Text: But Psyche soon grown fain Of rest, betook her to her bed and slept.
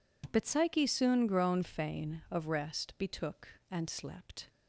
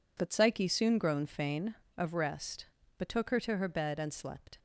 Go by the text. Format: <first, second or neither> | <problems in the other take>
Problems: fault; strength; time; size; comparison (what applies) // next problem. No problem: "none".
second | skips "her to her bed"; at 3.5 s